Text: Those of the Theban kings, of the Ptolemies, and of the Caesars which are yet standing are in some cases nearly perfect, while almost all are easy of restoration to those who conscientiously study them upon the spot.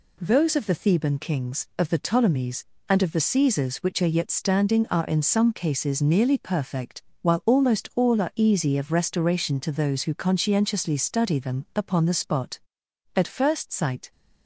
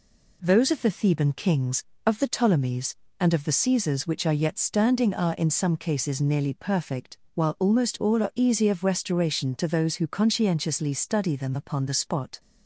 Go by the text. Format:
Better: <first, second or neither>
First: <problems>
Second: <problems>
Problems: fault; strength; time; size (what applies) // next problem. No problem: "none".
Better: second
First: goes on to say "At first sight"; noticeable; from 13.1 s on; 0.96 s long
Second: none